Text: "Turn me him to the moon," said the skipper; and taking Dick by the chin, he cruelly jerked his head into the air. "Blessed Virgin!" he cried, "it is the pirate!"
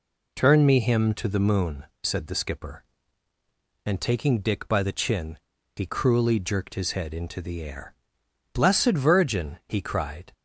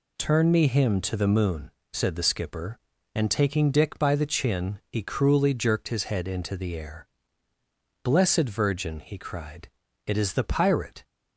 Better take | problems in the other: second | stops before "it is the pirate"; at 10.3 s

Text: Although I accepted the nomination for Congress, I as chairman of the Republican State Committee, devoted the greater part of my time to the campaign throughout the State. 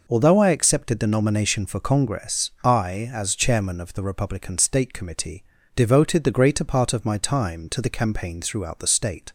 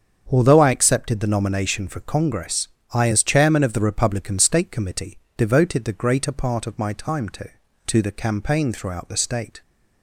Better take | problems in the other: first | starts louder than the rest; strong; until 1.3 s; 7 dB // says "to" twice; at 7.8 s

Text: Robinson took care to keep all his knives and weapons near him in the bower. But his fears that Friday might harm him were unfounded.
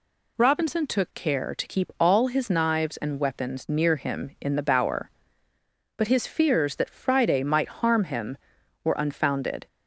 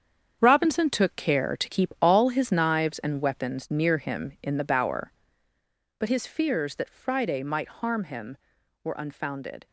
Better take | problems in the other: first | gets quieter; strong; throughout; 10 dB

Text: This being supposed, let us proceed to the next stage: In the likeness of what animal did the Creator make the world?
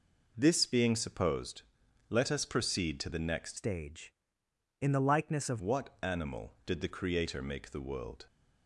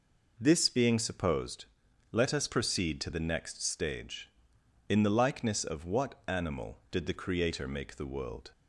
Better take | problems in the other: second | changes voice from "stage" to "of"; from 3.5 to 5.5 s; 2.0 s long

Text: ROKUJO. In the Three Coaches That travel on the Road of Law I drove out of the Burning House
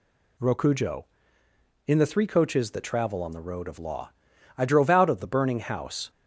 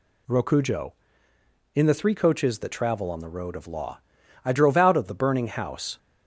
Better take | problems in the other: neither | pauses between "Law" and "I"; the same in both

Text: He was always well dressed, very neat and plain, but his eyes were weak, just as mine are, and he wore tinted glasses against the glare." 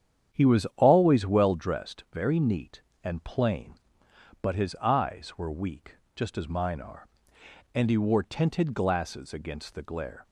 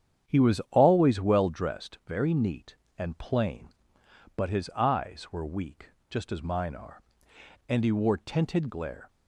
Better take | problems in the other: first | starts louder than the rest; strong; until 1.3 s; 9 dB; strong in the first // skips "glasses against the"; at 8.6 s

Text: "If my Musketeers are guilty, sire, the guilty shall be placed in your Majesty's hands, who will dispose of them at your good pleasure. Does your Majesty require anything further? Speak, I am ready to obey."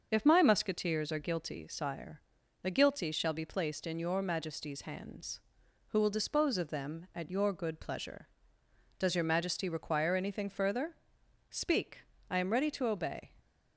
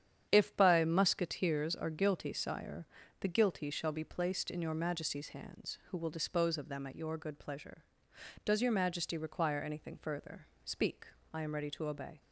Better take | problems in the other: first | starts louder than the rest; strong; until 1.3 s; 9.5 dB; also in the first // says "by" for "my"; at 0.5 s

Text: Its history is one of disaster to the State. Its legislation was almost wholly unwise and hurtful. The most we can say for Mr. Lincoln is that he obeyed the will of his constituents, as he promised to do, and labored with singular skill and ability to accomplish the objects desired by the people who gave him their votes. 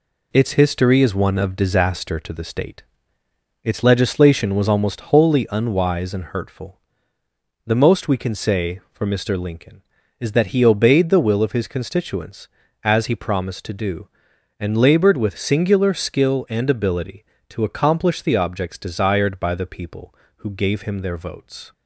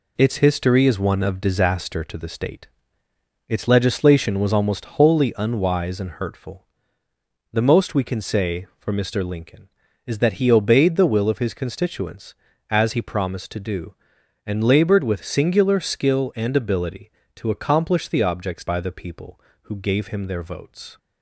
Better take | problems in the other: first | skips "desired"; at 18.6 s

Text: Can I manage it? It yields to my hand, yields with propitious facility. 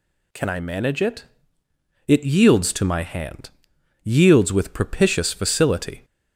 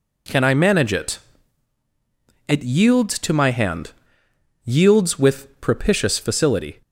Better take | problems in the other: neither | none

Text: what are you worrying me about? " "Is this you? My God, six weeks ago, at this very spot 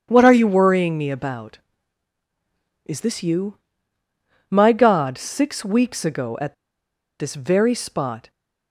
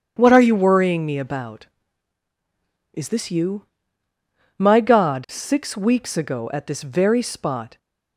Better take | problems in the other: second | pauses between "at" and "this"; noticeable; at 6.5 s; 0.65 s long

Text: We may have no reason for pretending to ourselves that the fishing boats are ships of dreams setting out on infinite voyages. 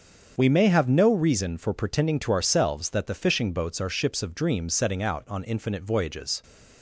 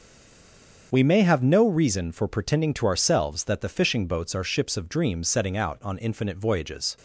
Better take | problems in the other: first | stays silent before the first word; slight; until 0.9 s; 0.9 s long // starts louder than the rest; strong; until 1.9 s; 7 dB; strong in the first

